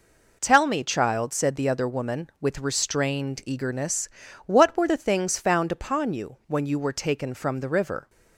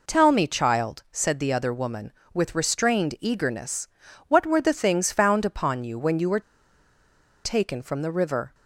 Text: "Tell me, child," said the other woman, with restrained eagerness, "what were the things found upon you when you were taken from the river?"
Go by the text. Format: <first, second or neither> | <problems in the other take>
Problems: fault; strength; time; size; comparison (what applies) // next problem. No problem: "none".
first | pauses between "were" and "taken"; at 6.3 s; 1.0 s long